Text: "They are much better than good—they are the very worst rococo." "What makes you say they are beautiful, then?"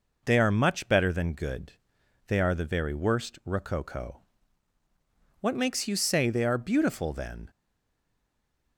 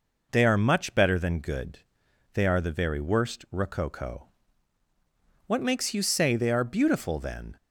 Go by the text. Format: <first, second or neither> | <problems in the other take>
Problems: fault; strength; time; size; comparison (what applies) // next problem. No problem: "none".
second | stays silent after the last word; noticeable; from 7.4 s on; 1.3 s long